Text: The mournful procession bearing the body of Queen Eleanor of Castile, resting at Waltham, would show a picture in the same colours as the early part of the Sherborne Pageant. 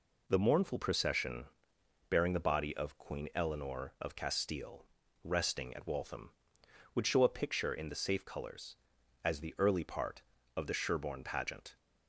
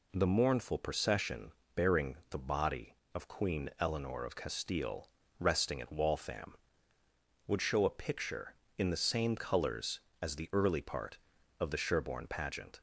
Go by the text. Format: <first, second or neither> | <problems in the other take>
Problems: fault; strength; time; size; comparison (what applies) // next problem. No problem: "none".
second | pauses between "procession" and "bearing"; noticeable; at 1.4 s; 0.62 s long; slight in the second // says "safe" for "same"; at 7.9 s